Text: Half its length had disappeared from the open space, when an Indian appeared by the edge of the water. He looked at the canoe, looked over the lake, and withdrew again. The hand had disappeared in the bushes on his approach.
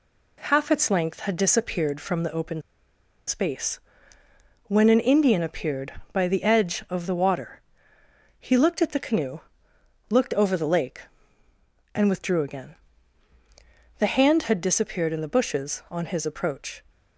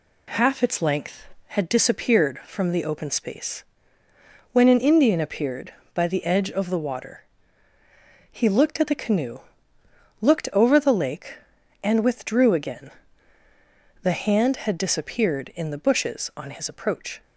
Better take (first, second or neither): second